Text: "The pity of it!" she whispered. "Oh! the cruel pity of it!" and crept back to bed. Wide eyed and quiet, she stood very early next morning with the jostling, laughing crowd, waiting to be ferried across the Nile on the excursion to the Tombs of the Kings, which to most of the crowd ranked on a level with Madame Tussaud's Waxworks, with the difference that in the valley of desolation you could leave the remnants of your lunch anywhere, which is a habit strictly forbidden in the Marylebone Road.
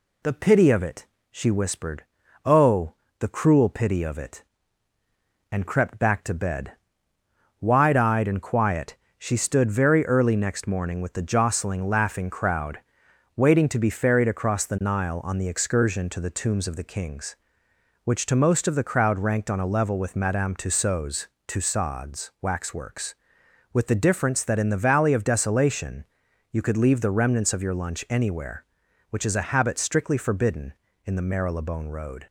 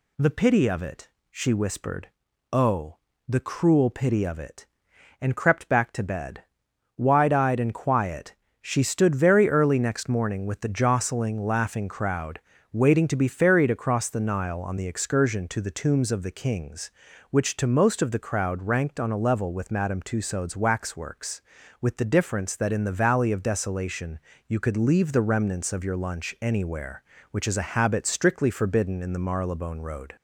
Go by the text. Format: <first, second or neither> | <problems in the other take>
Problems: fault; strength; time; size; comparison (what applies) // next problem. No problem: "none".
second | says "Tussaud's" twice; at 21.4 s // pauses between "desolation" and "you"; at 26.0 s; 0.44 s long; slight in the second